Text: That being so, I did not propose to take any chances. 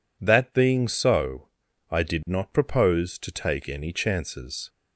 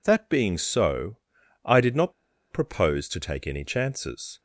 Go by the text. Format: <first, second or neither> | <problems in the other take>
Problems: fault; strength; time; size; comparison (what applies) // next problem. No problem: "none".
first | pauses between "not" and "propose"; at 2.1 s; 0.39 s long